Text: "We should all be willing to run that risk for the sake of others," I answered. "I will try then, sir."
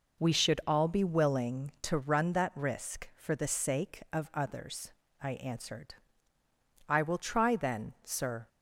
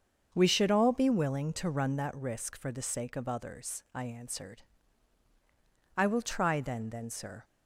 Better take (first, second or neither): first